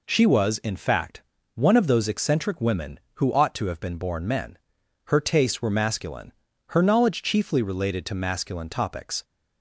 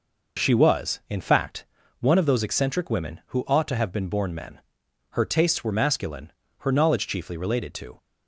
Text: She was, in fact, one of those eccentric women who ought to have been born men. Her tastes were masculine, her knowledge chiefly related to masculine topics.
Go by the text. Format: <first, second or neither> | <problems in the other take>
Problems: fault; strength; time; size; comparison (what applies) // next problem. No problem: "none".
first | stops before "masculine topics"; at 7.9 s